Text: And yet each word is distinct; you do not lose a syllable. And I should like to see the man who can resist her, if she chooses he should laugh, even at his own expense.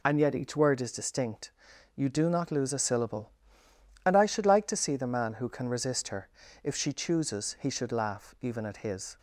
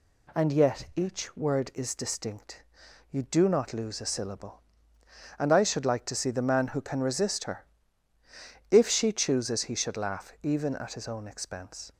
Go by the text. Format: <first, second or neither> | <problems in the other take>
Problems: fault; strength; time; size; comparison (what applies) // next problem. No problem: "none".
second | stops before "own expense"; at 9.1 s